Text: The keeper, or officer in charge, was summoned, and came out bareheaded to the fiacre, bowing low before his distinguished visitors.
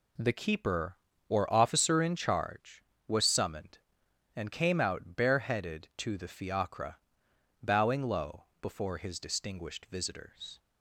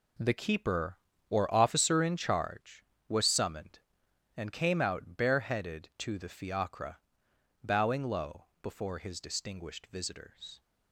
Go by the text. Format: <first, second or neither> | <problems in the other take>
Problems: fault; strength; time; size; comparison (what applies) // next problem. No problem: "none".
first | gets quieter; strong; throughout; 10 dB // pauses between "low" and "before"; slight; at 8.4 s; 0.18 s long; slight in the first